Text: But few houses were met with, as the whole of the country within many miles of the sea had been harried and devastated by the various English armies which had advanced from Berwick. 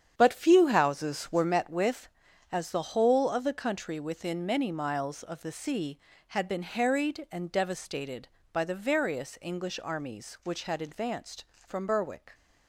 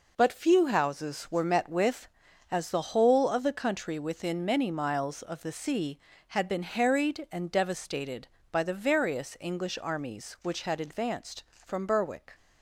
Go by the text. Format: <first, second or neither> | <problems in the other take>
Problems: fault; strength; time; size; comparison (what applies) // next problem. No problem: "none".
second | starts louder than the rest; strong; until 1.6 s; 8.5 dB